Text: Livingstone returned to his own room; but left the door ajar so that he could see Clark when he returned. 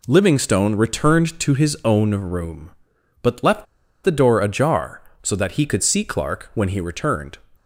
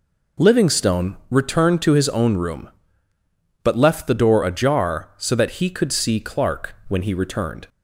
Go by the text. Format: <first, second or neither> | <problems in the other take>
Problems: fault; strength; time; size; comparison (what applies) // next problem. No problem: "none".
second | pauses between "left" and "the"; at 3.6 s; 0.40 s long